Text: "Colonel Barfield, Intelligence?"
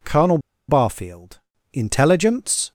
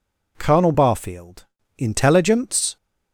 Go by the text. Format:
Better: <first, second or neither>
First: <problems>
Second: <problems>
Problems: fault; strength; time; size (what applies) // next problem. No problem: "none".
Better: second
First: pauses between "Colonel" and "Barfield"; slight; at 0.3 s; 0.30 s long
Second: none